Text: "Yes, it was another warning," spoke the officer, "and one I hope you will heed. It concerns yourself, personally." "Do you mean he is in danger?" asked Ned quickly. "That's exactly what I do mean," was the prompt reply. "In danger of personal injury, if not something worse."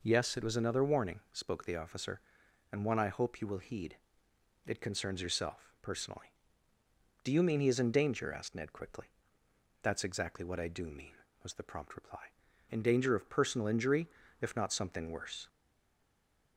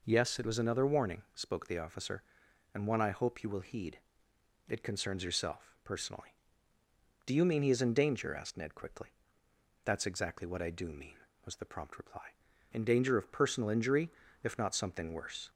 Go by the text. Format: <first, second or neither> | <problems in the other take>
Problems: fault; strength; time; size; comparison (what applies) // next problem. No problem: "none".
second | stays silent after the last word; from 15.4 s on; 1.1 s long